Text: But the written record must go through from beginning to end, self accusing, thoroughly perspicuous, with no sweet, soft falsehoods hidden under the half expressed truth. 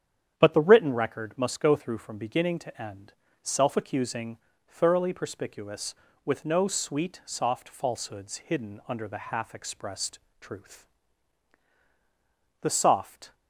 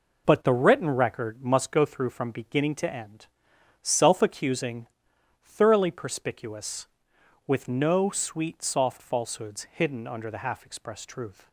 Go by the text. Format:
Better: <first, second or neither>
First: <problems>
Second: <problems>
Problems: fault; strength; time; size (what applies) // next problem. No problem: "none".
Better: second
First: starts louder than the rest; strong; until 1.3 s; 9 dB // pauses between "expressed" and "truth"; slight; at 10.1 s; 0.22 s long // goes on to say "The soft"; noticeable; from 12.6 s on; 0.72 s long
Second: none